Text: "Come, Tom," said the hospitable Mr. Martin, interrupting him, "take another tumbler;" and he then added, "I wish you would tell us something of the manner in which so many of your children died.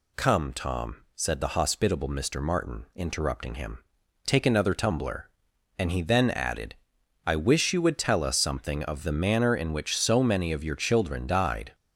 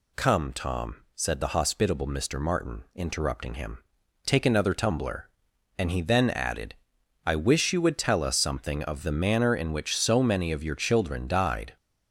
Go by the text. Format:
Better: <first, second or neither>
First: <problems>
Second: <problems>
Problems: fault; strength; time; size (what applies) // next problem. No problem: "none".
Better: neither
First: none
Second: none